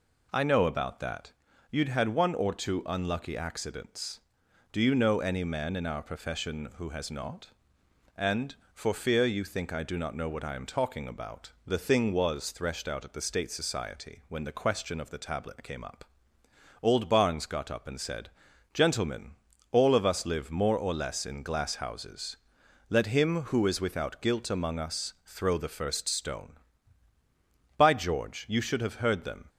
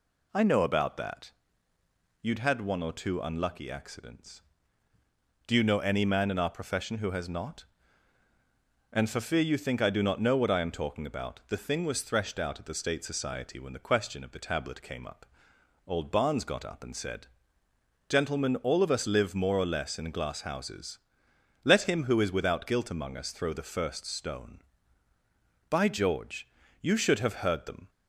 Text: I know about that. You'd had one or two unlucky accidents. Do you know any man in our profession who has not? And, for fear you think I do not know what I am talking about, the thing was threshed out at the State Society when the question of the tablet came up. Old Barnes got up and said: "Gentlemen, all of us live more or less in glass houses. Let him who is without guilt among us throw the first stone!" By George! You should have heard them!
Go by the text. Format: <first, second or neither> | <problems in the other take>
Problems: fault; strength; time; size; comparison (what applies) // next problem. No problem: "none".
neither | none